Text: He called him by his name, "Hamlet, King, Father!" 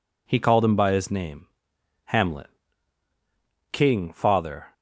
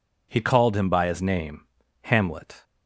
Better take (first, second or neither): first